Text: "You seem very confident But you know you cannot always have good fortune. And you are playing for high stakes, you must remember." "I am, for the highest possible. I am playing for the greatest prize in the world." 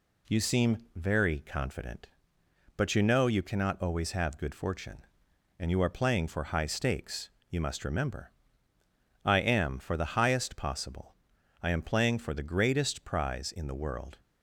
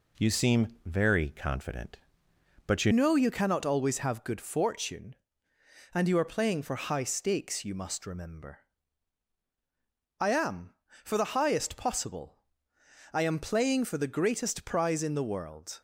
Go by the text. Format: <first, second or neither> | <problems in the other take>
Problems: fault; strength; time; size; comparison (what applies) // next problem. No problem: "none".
first | pauses between "seem" and "very"; slight; at 0.6 s; 0.18 s long; slight in the first // changes voice at "know"; from 2.9 s on; 12.9 s long